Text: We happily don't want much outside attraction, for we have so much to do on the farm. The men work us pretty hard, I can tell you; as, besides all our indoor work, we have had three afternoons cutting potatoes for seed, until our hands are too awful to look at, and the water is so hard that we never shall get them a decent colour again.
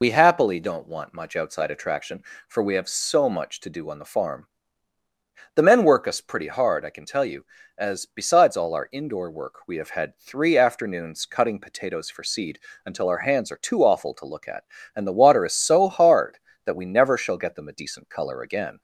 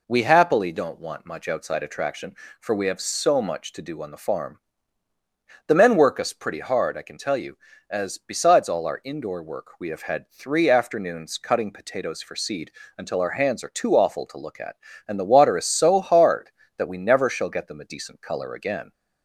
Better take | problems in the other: second | loses the start of "We"; at 0.0 s; 75 ms

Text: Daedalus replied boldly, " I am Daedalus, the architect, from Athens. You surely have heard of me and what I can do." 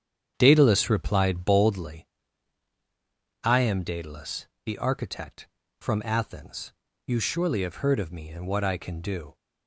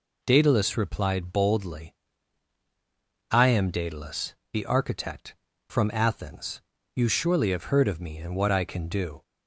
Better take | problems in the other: second | starts louder than the rest; strong; until 2.0 s; 8.5 dB

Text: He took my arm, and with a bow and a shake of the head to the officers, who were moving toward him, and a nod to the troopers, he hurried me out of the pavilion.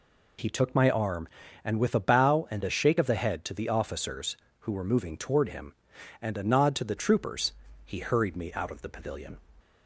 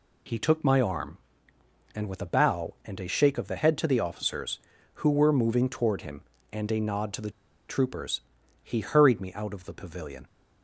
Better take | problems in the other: first | pauses between "the" and "troopers"; at 7.3 s; 0.37 s long

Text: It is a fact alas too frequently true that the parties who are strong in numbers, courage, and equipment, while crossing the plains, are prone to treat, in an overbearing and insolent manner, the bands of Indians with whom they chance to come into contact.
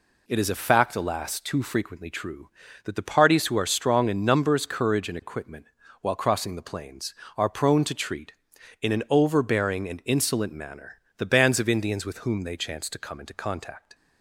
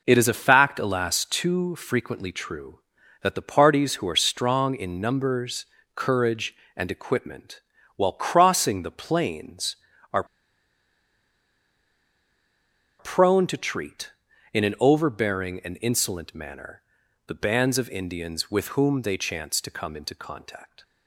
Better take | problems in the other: first | pauses between "are" and "prone"; strong; at 10.2 s; 2.7 s long

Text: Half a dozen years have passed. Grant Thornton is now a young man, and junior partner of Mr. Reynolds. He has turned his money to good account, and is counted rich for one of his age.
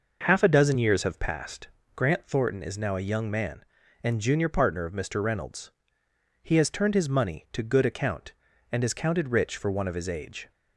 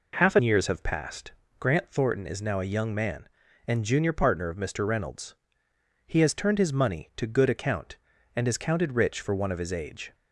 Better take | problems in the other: first | skips "dozen"; at 0.3 s

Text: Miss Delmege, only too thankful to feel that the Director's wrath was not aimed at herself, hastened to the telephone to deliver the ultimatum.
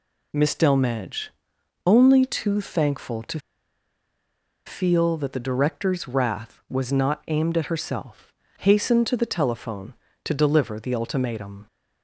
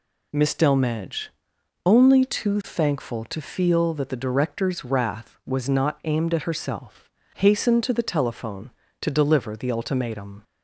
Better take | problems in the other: second | pauses between "to" and "feel"; strong; at 3.3 s; 1.2 s long

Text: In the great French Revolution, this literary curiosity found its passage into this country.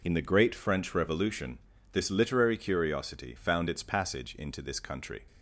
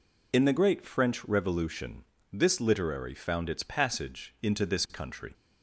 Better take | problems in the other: first | skips "curiosity"; at 3.1 s

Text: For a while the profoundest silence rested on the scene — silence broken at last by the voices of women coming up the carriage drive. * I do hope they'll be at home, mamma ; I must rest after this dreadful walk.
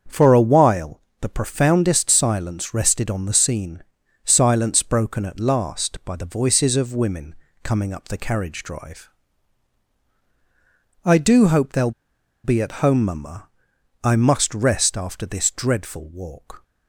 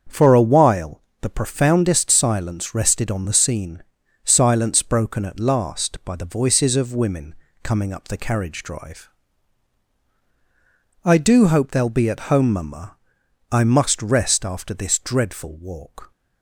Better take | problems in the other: second | starts louder than the rest; until 1.2 s; 7 dB; also in the second // pauses between "while" and "the"; slight; at 1.0 s; 0.20 s long; slight in the second // pauses between "women" and "coming"; slight; at 7.3 s; 0.28 s long; slight in the second // pauses between "they'll" and "be"; noticeable; at 11.9 s; 0.53 s long

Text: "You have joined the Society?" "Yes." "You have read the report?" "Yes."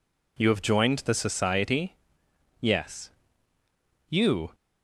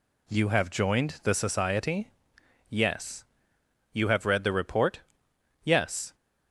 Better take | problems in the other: second | stops before "have read the report Yes"; at 4.5 s

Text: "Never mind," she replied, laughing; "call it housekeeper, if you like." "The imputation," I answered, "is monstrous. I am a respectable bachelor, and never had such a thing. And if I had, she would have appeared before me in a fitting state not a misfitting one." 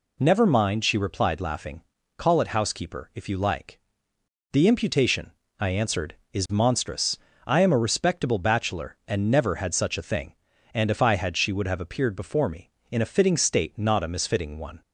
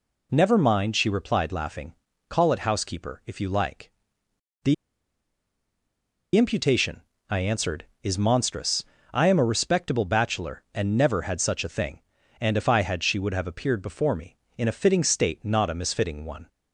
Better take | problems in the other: first | pauses between "The" and "imputation"; strong; at 4.7 s; 1.6 s long

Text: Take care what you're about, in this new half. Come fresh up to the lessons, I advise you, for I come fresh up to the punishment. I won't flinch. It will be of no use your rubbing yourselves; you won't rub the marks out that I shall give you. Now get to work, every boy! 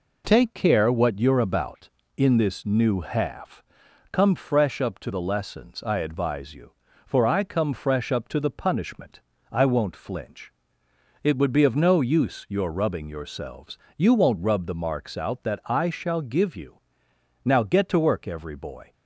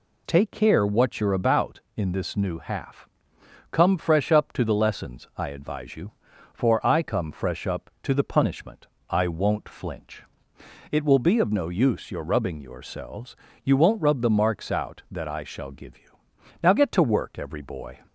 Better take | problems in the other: second | says "would" for "will"; at 11.3 s

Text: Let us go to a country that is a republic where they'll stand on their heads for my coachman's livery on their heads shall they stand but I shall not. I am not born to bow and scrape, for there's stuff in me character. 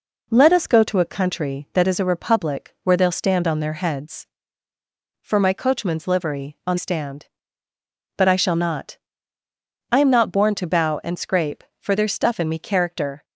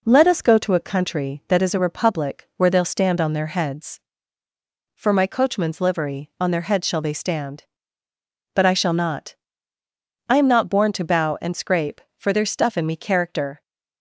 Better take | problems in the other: second | skips "their heads shall they"; at 6.7 s

